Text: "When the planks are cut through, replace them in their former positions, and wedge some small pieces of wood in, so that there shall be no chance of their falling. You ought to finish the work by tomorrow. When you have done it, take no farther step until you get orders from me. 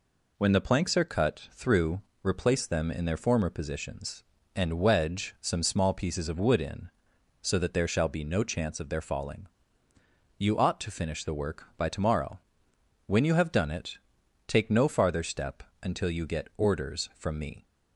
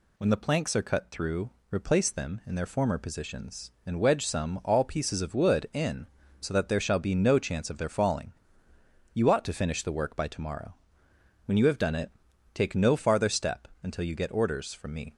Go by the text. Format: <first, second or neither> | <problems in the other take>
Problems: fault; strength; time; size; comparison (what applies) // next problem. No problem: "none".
first | says "all" for "small"; at 4.6 s // pauses between "step" and "until"; slight; at 13.6 s; 0.16 s long; slight in the first